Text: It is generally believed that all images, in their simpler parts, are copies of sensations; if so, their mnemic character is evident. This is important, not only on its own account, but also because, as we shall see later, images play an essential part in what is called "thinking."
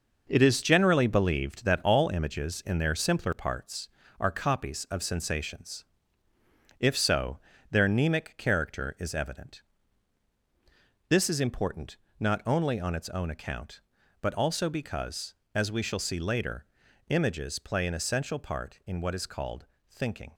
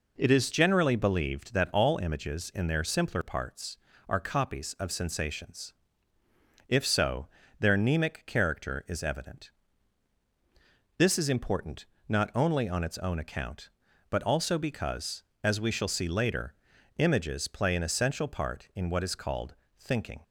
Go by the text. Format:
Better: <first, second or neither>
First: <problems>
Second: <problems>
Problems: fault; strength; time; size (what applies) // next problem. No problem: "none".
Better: second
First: gets quieter; throughout; 7 dB // pauses between "called" and "thinking"; slight; at 19.6 s; 0.26 s long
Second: pauses between "called" and "thinking"; slight; at 19.5 s; 0.26 s long